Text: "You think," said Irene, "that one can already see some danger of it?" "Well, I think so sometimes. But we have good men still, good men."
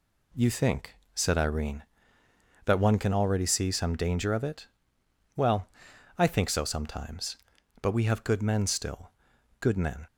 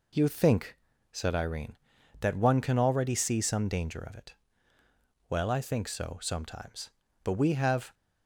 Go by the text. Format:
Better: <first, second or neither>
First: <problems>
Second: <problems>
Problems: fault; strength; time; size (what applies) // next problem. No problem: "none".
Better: first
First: none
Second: stops before "good men still good men"; at 7.9 s